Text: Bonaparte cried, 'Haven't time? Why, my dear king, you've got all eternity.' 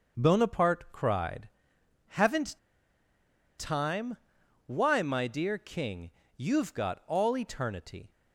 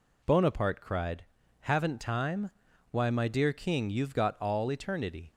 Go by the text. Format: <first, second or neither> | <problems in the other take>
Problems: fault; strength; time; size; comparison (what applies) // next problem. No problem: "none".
second | starts louder than the rest; until 1.2 s; 6.5 dB // pauses between "Haven't" and "time"; at 2.5 s; 0.99 s long